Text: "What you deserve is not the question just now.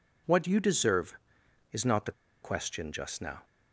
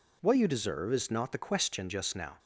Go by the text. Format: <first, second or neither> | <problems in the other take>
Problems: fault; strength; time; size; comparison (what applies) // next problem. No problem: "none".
second | pauses between "the" and "question"; slight; at 2.1 s; 0.30 s long